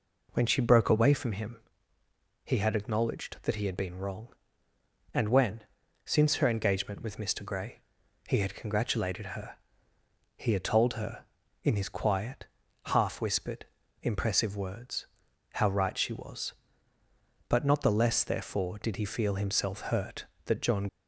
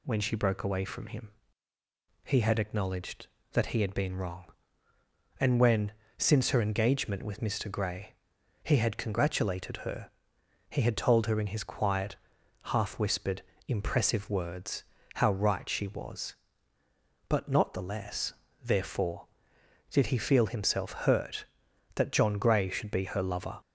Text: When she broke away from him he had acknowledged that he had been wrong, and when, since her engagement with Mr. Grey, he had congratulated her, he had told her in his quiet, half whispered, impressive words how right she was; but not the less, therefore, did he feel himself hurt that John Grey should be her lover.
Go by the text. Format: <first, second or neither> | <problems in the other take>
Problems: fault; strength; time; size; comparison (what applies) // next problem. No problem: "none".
second | pauses between "him" and "he"; noticeable; at 1.5 s; 0.86 s long; noticeable in the second // pauses between "words" and "how"; noticeable; at 15.0 s; 0.48 s long; slight in the second // stops before "Grey should be her lover"; at 20.8 s